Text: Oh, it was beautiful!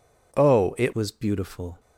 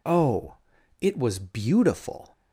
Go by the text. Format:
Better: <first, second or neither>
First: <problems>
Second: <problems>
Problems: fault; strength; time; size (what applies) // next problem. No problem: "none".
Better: second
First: changes voice at "was"; from 0.9 s on; 0.8 s long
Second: none